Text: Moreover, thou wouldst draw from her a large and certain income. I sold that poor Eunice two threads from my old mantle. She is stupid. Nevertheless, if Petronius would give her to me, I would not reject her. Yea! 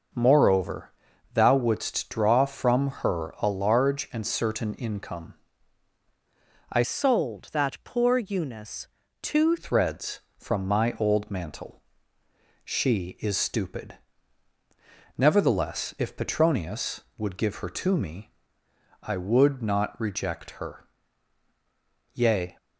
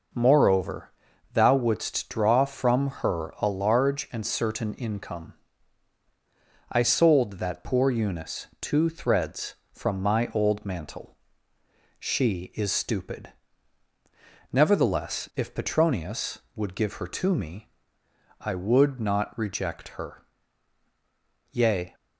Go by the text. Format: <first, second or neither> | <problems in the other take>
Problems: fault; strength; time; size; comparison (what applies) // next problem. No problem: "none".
second | starts louder than the rest; until 1.5 s; 6 dB // changes voice from "sold" to "two"; from 6.8 to 9.5 s; 2.7 s long // pauses between "Eunice" and "two"; slight; at 8.8 s; 0.34 s long